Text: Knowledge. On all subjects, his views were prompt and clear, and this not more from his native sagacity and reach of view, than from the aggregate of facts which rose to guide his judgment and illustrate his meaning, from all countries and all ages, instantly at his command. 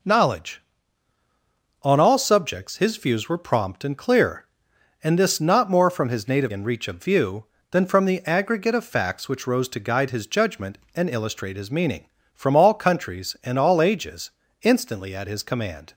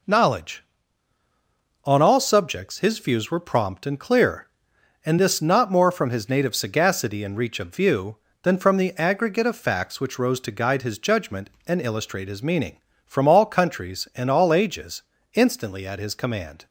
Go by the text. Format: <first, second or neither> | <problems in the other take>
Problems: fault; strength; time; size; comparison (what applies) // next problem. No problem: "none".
second | skips "sagacity"; at 6.5 s